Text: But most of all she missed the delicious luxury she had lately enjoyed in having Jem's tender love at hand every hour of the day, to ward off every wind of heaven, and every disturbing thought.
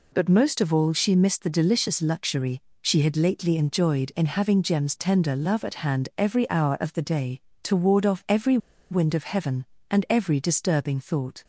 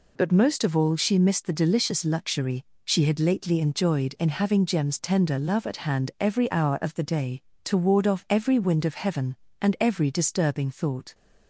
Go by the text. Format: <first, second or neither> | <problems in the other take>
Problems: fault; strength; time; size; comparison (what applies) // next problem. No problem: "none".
second | pauses between "luxury" and "she"; slight; at 2.6 s; 0.20 s long; slight in the second // pauses between "every" and "wind"; slight; at 8.5 s; 0.33 s long